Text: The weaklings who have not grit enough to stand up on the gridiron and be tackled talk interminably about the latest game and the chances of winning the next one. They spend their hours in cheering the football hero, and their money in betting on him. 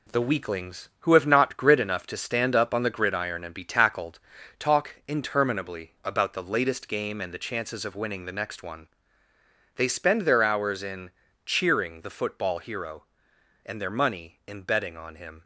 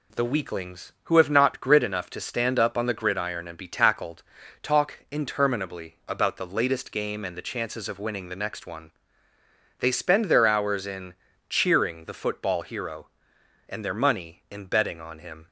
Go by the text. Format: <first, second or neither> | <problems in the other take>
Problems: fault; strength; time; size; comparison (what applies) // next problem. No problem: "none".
second | gets quieter; throughout; 7 dB // pauses between "tackled" and "talk"; at 4.1 s; 0.38 s long; also in the second // pauses between "in" and "cheering"; slight; at 11.0 s; 0.36 s long; slight in the second